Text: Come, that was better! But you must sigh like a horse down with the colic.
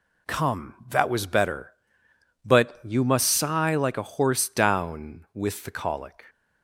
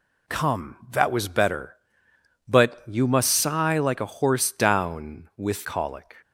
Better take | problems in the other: first | skips "the"; at 5.6 s

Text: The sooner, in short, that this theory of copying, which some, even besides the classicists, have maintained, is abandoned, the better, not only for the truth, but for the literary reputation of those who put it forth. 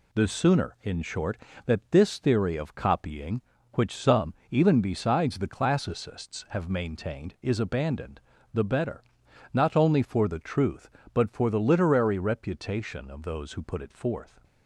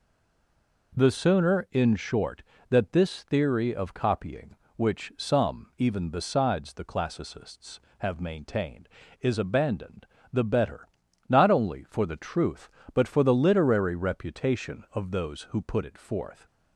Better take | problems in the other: first | stays silent before the first word; slight; until 0.9 s; 0.9 s long

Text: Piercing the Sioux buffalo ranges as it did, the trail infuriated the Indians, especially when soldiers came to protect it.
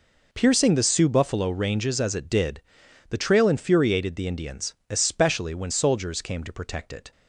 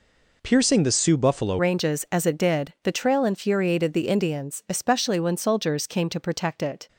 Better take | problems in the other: first | changes voice at "ranges"; from 1.5 s on; 5.3 s long

